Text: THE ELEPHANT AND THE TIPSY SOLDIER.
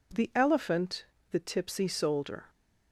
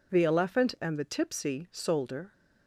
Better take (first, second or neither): second